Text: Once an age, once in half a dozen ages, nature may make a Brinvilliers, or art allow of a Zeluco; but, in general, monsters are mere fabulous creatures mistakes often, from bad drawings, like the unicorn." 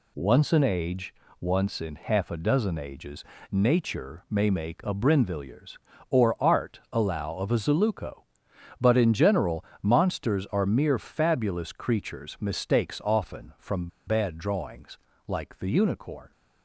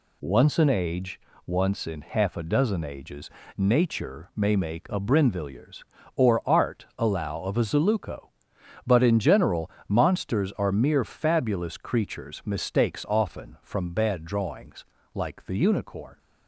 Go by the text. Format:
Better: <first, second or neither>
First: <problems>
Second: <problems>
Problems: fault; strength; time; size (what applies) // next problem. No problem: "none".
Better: second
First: pauses between "from" and "bad"; slight; at 13.8 s; 0.19 s long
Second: none